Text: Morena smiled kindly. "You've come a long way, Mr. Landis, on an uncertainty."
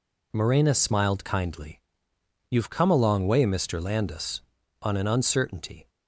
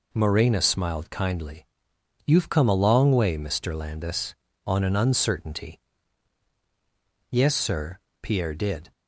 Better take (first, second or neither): first